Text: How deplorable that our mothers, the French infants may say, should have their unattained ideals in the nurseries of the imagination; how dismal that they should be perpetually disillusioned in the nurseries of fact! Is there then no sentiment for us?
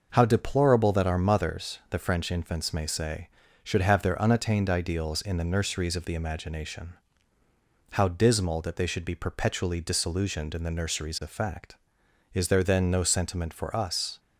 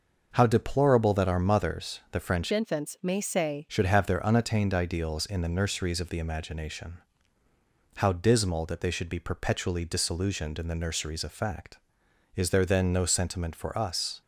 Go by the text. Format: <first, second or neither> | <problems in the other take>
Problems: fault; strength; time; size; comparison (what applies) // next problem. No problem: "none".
first | changes voice from "infants" to "say"; from 2.5 to 3.6 s; 1.1 s long